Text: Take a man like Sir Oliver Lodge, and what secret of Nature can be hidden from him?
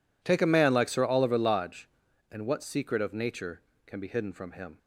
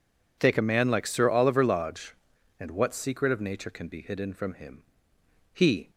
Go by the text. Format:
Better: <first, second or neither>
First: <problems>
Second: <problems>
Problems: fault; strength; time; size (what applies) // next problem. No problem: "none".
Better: first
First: none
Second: goes on to say "He"; slight; from 5.5 s on; 0.38 s long